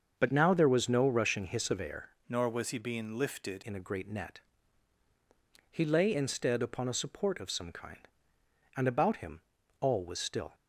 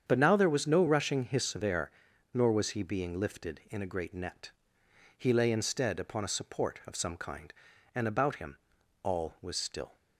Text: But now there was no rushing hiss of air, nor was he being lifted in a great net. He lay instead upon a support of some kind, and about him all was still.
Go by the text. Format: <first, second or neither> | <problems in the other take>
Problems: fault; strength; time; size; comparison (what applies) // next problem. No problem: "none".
second | starts louder than the rest; until 1.1 s; 6.5 dB; strong in the second // changes voice from "nor" to "lifted"; from 2.2 to 3.6 s; 1.4 s long // pauses between "him" and "all"; at 9.4 s; 0.40 s long; noticeable in the second